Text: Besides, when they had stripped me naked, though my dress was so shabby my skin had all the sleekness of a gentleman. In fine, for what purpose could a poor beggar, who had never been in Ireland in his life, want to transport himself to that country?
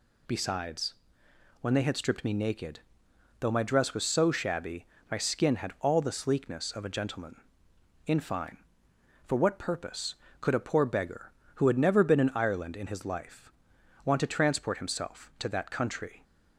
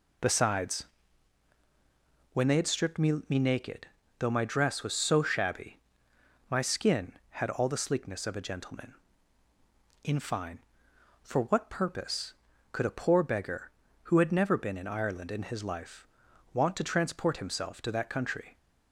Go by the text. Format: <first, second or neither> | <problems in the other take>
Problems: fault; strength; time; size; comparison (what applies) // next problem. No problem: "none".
first | says "me" twice; at 3.2 s // pauses between "shabby" and "my"; noticeable; at 5.7 s; 0.70 s long; slight in the first